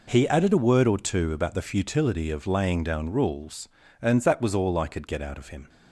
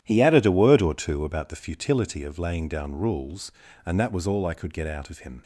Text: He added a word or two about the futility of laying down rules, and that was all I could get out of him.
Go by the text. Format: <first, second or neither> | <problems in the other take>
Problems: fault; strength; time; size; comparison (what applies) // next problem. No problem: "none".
first | starts louder than the rest; strong; until 1.7 s; 11 dB